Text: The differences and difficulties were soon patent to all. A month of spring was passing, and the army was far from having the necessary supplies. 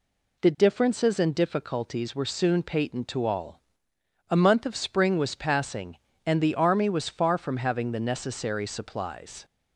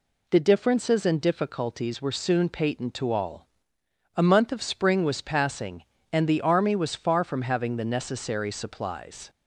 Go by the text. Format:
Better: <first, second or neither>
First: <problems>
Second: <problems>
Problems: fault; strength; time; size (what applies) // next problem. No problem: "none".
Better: neither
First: none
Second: none